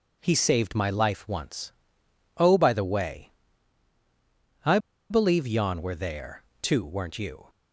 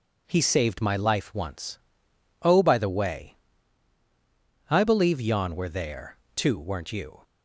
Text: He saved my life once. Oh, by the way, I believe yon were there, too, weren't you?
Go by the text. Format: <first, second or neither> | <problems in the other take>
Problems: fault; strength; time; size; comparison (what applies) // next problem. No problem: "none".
second | pauses between "I" and "believe"; slight; at 4.7 s; 0.32 s long